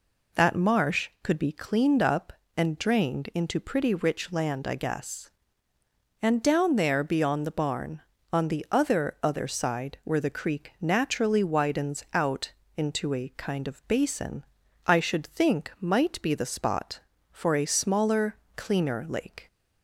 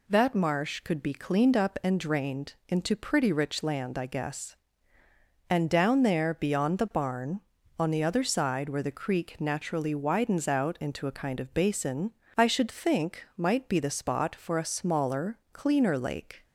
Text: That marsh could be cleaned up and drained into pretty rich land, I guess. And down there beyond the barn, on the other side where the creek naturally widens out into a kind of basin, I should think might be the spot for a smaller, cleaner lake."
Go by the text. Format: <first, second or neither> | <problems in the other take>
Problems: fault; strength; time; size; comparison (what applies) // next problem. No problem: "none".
second | says "other" twice; at 9.2 s // pauses between "out" and "into"; slight; at 12.5 s; 0.26 s long